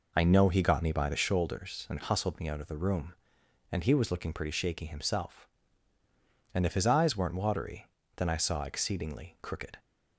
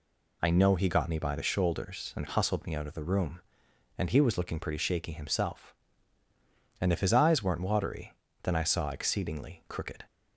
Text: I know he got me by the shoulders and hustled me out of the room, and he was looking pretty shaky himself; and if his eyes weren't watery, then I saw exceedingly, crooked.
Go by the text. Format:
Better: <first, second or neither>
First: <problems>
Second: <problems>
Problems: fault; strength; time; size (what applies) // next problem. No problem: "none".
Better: second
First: starts louder than the rest; noticeable; until 1.4 s; 4.5 dB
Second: none